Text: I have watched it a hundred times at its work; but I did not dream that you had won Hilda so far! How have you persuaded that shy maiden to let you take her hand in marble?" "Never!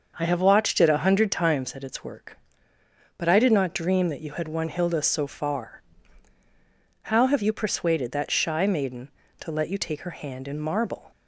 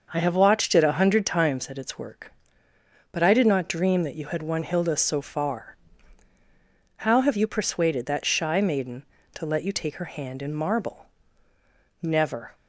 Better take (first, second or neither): second